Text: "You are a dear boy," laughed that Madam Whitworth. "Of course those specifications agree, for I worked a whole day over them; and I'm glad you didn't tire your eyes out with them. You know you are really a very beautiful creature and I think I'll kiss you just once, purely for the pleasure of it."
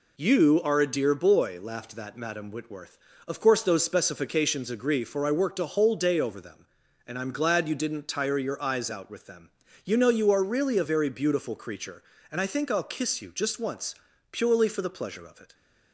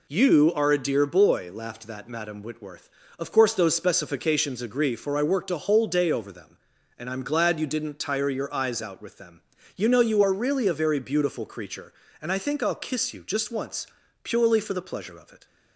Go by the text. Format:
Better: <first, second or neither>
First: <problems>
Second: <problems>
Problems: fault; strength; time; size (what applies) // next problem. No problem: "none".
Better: neither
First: none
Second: none